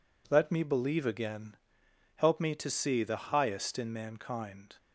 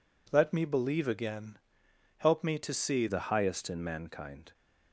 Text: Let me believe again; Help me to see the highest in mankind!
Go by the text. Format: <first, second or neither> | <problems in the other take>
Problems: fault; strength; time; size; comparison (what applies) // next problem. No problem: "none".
first | changes voice at "the"; from 3.0 s on; 1.5 s long